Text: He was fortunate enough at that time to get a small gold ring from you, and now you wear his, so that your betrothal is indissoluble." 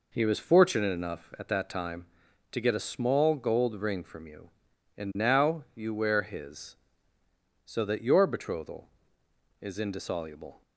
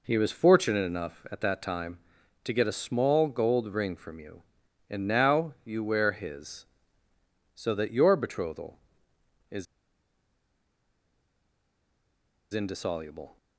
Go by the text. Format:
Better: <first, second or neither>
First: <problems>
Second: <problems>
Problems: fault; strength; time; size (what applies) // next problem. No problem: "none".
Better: first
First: none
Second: pauses between "is" and "indissoluble"; strong; at 9.6 s; 2.8 s long